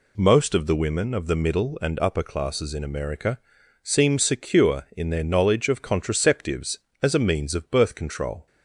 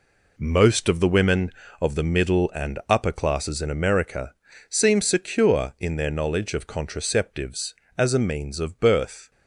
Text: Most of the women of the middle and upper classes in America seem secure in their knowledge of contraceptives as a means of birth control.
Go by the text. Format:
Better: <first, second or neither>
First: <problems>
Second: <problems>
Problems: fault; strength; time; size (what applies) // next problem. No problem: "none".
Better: first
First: pauses between "America" and "seem"; at 3.3 s; 0.44 s long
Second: pauses between "America" and "seem"; slight; at 4.3 s; 0.34 s long // stops before "control"; at 9.3 s